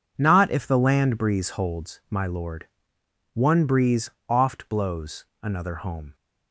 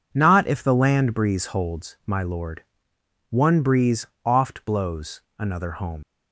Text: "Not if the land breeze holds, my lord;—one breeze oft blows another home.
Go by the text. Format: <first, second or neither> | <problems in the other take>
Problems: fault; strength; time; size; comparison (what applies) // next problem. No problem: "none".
first | pauses between "breeze" and "oft"; slight; at 4.0 s; 0.18 s long; slight in the first // pauses between "blows" and "another"; slight; at 5.2 s; 0.18 s long; slight in the first // leaves "home" unfinished; at 6.0 s; 80 ms